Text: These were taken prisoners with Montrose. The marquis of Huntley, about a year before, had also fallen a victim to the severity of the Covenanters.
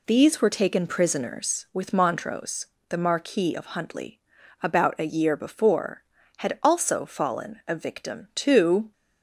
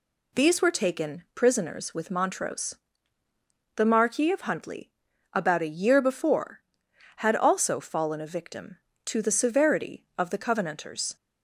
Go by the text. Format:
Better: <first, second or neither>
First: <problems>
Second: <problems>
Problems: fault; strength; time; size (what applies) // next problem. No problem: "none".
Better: second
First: stops before "the severity of the Covenanters"; at 8.9 s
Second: none